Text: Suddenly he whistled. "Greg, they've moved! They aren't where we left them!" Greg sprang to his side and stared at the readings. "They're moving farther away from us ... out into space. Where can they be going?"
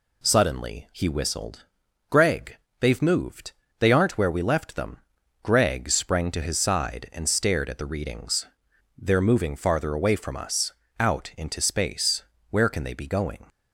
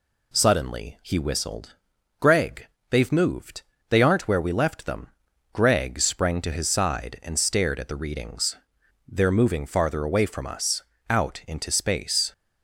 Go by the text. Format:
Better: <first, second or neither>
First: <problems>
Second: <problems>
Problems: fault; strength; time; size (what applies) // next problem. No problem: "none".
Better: first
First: none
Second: stops before "Where can they be going"; at 12.3 s